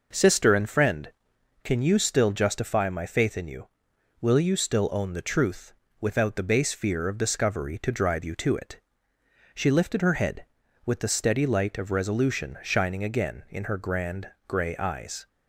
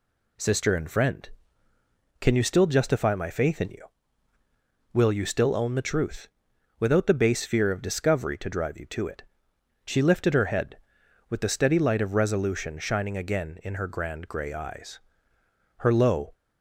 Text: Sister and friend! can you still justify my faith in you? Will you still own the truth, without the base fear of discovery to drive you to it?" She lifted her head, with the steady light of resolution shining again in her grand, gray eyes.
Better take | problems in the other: first | goes on to say "Her low"; from 15.7 s on; 0.56 s long

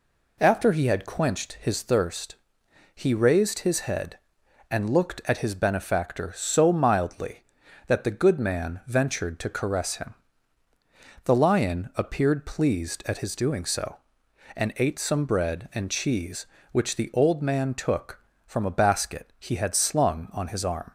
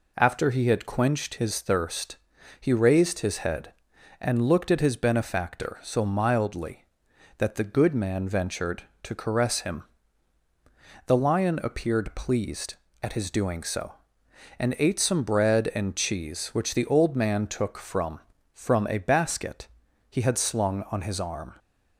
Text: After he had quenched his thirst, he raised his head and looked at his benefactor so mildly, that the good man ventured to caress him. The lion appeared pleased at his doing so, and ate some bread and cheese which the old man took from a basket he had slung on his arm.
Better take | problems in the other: first | says "from" twice; at 18.5 s // pauses between "basket" and "he"; at 19.6 s; 0.44 s long

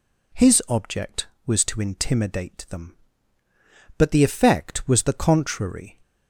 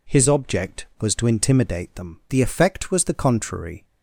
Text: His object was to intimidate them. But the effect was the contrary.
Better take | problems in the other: first | skips "But"; at 2.2 s

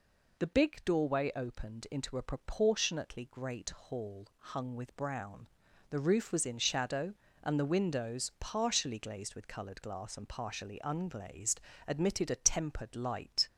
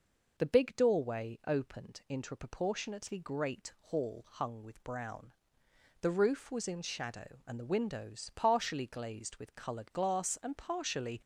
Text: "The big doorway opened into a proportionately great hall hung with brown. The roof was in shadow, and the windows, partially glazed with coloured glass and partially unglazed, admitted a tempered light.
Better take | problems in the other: first | stops before "unglazed admitted a tempered light"; at 11.2 s

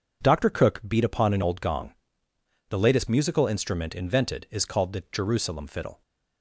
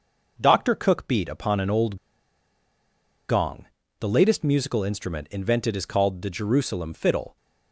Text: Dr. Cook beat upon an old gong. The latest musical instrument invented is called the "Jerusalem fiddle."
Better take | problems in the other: first | pauses between "old" and "gong"; strong; at 1.9 s; 1.3 s long

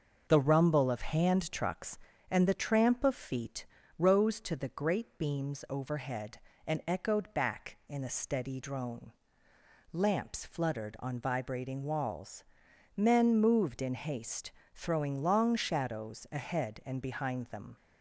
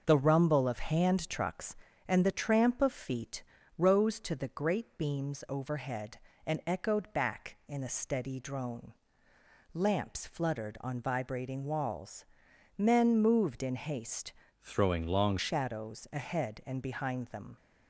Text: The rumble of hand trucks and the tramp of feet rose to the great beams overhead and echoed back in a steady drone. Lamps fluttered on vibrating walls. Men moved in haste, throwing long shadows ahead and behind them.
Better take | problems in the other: first | pauses between "feet" and "rose"; slight; at 3.4 s; 0.36 s long; slight in the first // changes voice from "throwing" to "long"; from 14.6 to 15.3 s; 0.7 s long

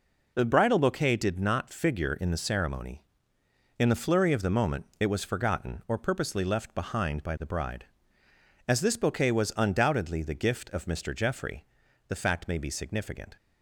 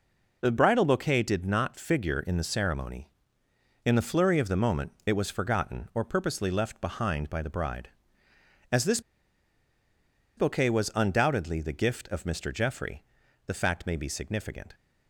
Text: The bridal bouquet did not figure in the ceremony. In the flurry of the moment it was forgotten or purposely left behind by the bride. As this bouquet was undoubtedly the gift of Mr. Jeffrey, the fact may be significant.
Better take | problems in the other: first | pauses between "this" and "bouquet"; strong; at 8.9 s; 1.3 s long

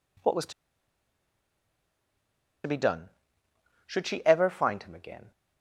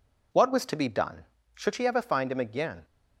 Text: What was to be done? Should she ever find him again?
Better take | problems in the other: second | pauses between "to" and "be"; strong; at 0.5 s; 2.1 s long

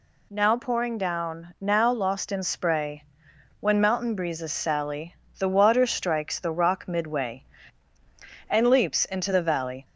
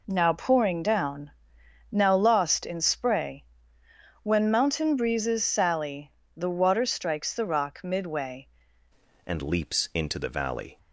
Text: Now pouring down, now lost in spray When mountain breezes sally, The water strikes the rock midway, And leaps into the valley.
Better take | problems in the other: first | pauses between "spray" and "When"; noticeable; at 3.4 s; 0.78 s long; noticeable in the first // changes voice at "And"; from 9.2 s on; 1.5 s long

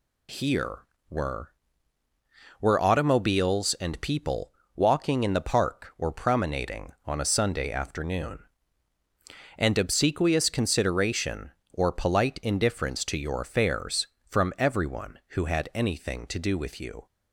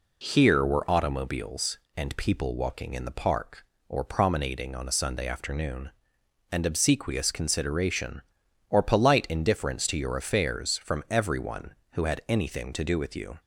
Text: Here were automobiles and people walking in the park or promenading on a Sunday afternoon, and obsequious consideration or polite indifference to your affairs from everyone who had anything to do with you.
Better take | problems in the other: second | says "were" twice; at 2.6 s // pauses between "people" and "walking"; slight; at 4.5 s; 0.24 s long

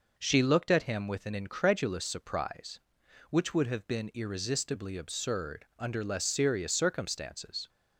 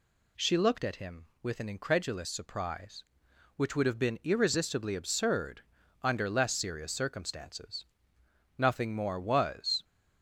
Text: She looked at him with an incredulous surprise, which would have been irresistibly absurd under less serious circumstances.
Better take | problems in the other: first | pauses between "absurd" and "under"; at 5.6 s; 0.40 s long // goes on to say "Nothing more was"; noticeable; from 8.5 s on; 1.2 s long

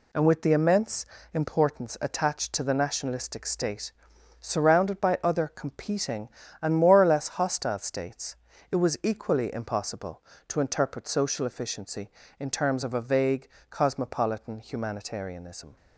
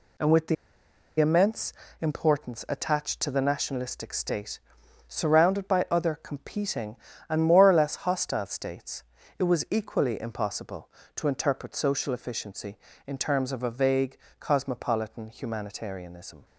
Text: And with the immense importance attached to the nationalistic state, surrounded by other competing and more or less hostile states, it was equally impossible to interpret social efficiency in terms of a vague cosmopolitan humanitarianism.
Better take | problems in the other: first | pauses between "the" and "immense"; noticeable; at 0.5 s; 0.64 s long // pauses between "immense" and "importance"; slight; at 1.7 s; 0.28 s long; slight in the first // pauses between "vague" and "cosmopolitan"; slight; at 14.1 s; 0.22 s long; slight in the first

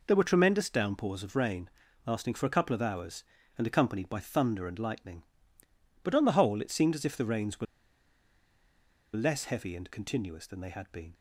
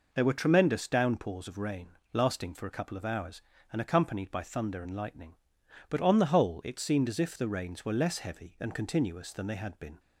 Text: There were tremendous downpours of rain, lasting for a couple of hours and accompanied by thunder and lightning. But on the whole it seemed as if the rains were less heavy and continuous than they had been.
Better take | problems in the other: second | pauses between "were" and "less"; strong; at 7.6 s; 1.5 s long

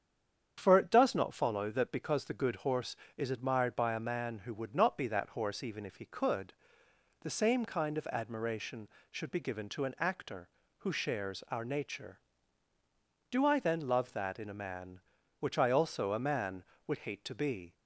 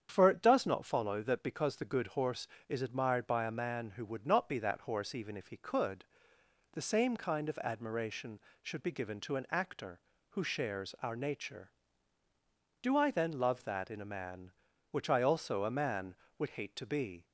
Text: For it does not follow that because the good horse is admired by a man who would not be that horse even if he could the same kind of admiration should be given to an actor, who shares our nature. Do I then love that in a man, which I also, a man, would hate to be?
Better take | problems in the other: second | stays silent before the first word; slight; until 0.5 s; 0.5 s long // starts louder than the rest; strong; until 1.5 s; 8 dB; strong in the second // pauses between "could" and "the"; noticeable; at 6.5 s; 0.68 s long; noticeable in the second

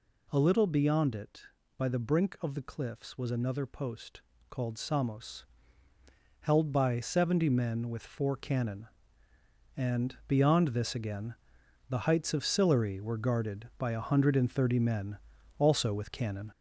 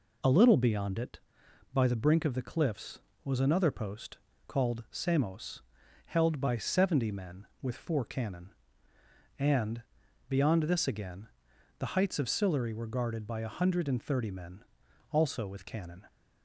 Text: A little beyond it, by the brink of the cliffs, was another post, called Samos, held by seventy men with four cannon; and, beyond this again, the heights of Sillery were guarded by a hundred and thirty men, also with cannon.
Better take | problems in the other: second | gets louder; noticeable; throughout; 4.5 dB

